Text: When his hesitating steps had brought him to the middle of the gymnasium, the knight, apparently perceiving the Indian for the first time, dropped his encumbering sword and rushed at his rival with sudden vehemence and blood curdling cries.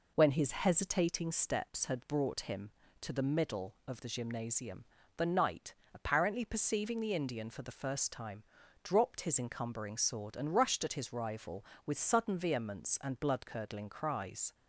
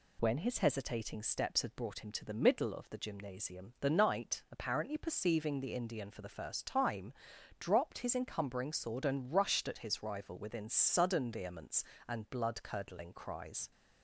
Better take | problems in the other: first | says "within" for "with"; at 10.3 s

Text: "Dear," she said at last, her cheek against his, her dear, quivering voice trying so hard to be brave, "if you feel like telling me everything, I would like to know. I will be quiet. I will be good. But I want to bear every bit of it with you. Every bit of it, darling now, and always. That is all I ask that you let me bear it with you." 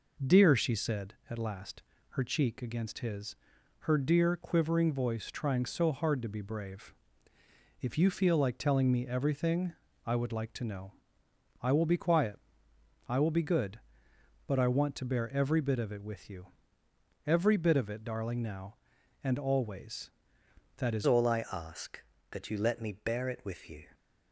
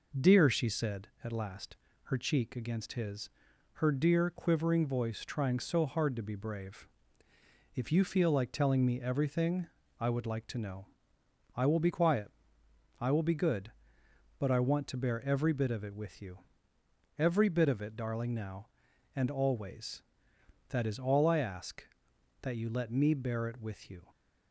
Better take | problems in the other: second | changes voice at "all"; from 21.0 s on; 2.8 s long

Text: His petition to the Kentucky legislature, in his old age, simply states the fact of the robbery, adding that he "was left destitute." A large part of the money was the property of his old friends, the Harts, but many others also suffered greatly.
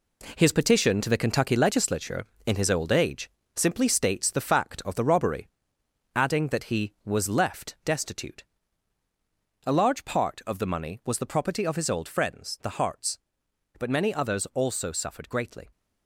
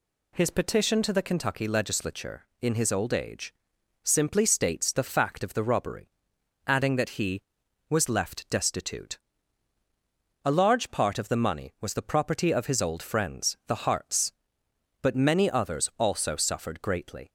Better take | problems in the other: second | gets quieter; strong; throughout; 7.5 dB

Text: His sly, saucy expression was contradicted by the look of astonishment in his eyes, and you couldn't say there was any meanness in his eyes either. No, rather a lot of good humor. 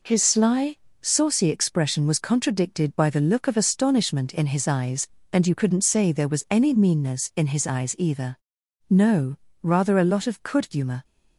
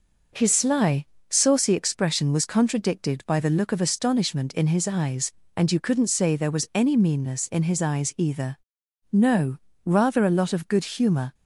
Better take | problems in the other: second | says "could" for "good"; at 10.4 s

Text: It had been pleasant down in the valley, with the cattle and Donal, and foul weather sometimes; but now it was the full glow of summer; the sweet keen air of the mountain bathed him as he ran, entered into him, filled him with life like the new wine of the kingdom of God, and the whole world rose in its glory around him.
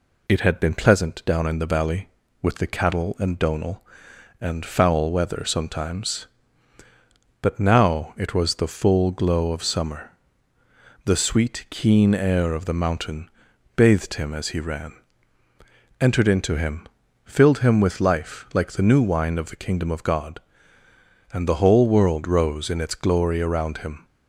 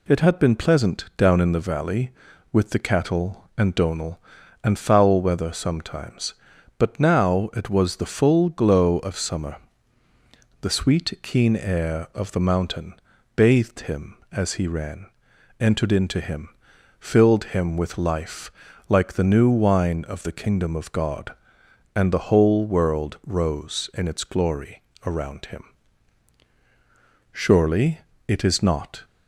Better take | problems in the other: first | pauses between "mountain" and "bathed"; at 12.9 s; 0.42 s long; noticeable in the first // pauses between "life" and "like"; at 18.4 s; 0.38 s long // pauses between "glory" and "around"; slight; at 24.8 s; 0.24 s long // goes on to say "Surely it is not"; from 27.4 s on; 1.6 s long

